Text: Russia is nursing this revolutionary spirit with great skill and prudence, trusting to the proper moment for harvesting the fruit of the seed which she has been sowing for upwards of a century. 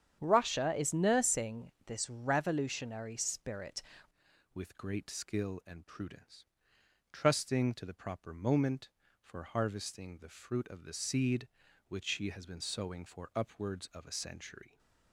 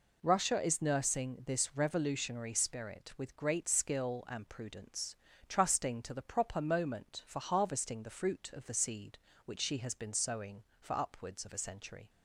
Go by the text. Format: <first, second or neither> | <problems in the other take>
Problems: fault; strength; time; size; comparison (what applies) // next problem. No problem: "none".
second | starts louder than the rest; strong; until 1.2 s; 9 dB // pauses between "nursing" and "this"; slight; at 1.7 s; 0.16 s long // changes voice at "with"; from 4.5 s on; 10.2 s long